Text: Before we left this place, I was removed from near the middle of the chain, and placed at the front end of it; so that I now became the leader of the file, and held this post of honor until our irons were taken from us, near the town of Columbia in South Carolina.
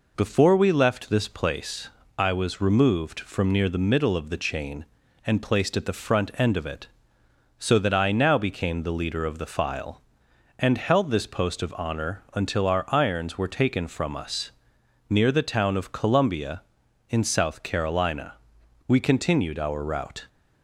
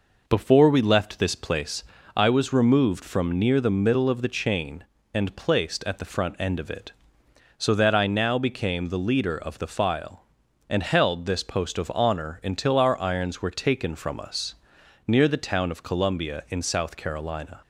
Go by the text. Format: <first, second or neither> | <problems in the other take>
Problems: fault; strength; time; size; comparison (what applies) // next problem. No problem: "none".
second | goes on to say "We continued our route"; from 18.8 s on; 1.4 s long